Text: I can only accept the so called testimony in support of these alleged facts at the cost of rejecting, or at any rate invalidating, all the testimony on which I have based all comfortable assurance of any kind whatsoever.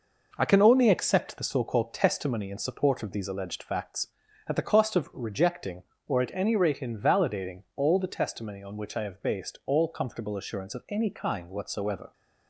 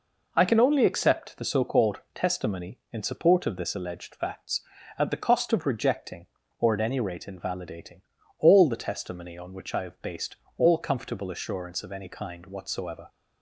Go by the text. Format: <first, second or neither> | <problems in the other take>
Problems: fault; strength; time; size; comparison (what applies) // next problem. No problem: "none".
first | pauses between "called" and "testimony"; slight; at 1.9 s; 0.16 s long // says "this" for "these"; at 3.5 s // pauses between "based" and "all"; slight; at 10.3 s; 0.20 s long